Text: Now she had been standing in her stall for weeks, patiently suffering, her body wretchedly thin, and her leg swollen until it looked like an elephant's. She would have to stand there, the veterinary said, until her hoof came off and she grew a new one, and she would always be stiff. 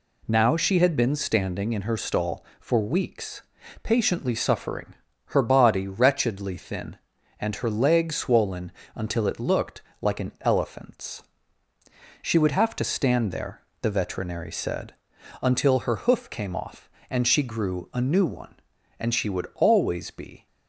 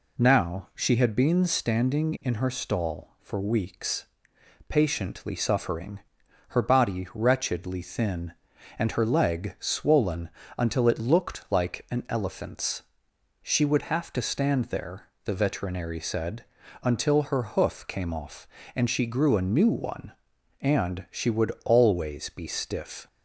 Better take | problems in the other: second | pauses between "swollen" and "until"; slight; at 8.7 s; 0.24 s long; slight in the second // pauses between "looked" and "like"; slight; at 9.8 s; 0.18 s long // stops before "stiff"; at 20.4 s

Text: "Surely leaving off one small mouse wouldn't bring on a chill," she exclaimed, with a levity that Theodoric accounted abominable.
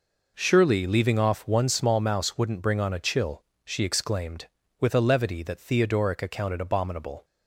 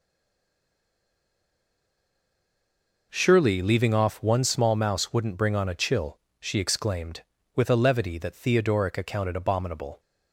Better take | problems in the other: first | stays silent before the first word; strong; until 3.1 s; 3.1 s long

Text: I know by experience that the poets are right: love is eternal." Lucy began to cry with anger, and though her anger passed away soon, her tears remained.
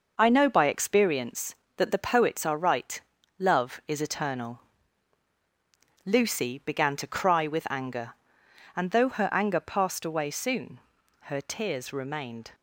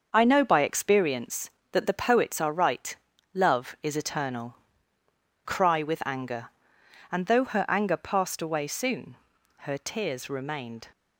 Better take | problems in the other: first | starts louder than the rest; until 1.1 s; 6.5 dB // skips "Lucy began to"; at 5.0 s

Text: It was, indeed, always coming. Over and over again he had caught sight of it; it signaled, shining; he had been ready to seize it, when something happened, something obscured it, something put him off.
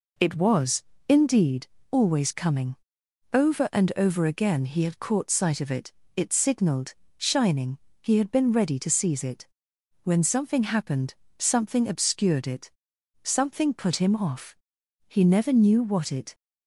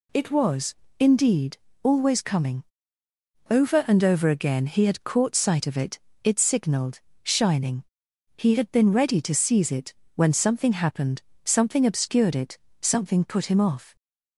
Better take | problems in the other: second | goes on to say "He never knew what it"; noticeable; from 15.0 s on; 1.2 s long

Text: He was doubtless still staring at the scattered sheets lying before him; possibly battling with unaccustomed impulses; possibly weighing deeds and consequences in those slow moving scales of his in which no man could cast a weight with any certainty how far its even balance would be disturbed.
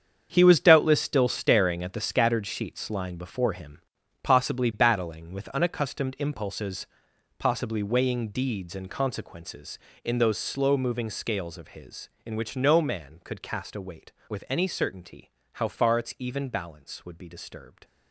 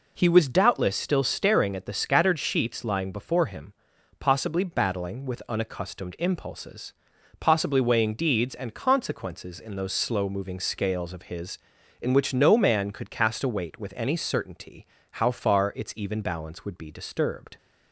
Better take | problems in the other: second | gets quieter; strong; throughout; 11.5 dB // pauses between "certainty" and "how"; slight; at 15.2 s; 0.28 s long; slight in the second

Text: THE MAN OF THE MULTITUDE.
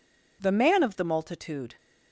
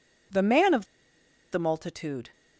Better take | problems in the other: first | pauses between "OF" and "THE"; noticeable; at 0.8 s; 0.67 s long

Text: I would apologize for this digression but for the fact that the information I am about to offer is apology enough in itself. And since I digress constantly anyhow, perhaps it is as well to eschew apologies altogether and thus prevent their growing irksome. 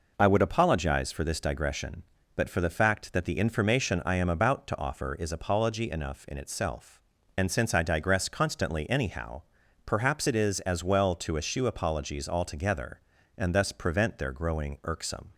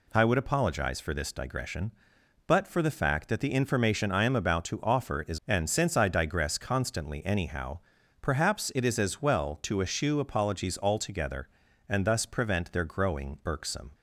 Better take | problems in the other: first | skips "apology enough in itself"; at 5.4 s

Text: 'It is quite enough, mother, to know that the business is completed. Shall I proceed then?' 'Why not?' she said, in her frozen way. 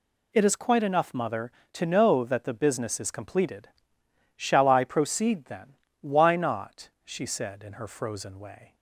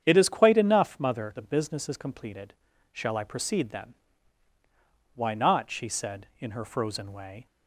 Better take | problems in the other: first | starts louder than the rest; strong; until 1.0 s; 8.5 dB // skips "to know that"; at 1.3 s

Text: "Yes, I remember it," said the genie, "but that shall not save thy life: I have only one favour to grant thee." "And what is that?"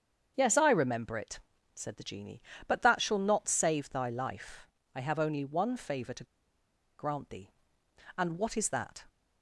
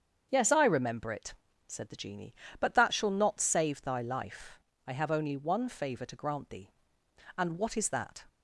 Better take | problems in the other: second | starts louder than the rest; strong; until 1.3 s; 7.5 dB; strong in the second // pauses between "to" and "grant"; noticeable; at 6.2 s; 0.73 s long

